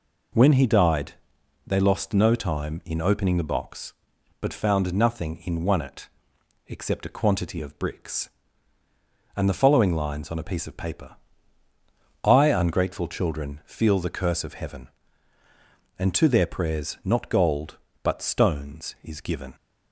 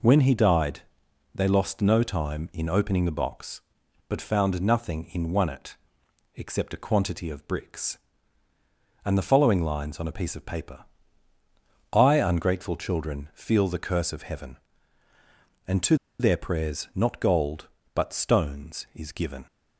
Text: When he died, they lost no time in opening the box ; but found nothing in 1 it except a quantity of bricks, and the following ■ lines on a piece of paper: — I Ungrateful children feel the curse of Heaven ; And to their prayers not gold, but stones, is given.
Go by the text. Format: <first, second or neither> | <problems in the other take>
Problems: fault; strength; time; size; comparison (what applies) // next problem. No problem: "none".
first | pauses between "it" and "except"; noticeable; at 5.7 s; 0.58 s long; noticeable in the first // pauses between "to" and "their"; slight; at 15.9 s; 0.24 s long